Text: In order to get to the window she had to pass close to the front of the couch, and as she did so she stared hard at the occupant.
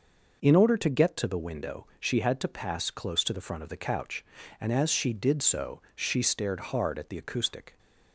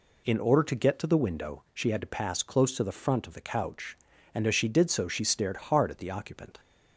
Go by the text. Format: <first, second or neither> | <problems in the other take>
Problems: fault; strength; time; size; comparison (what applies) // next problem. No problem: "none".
second | says "acoustic" for "occupant"; at 7.1 s